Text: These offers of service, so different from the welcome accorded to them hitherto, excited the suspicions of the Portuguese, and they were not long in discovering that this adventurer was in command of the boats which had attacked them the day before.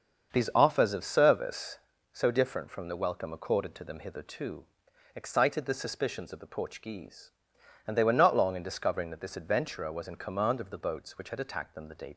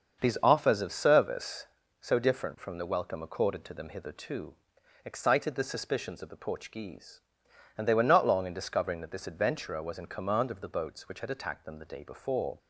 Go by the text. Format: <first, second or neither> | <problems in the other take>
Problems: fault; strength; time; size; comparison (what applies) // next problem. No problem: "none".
second | starts louder than the rest; until 1.3 s; 6.5 dB; also in the second // stops before "before"; at 12.1 s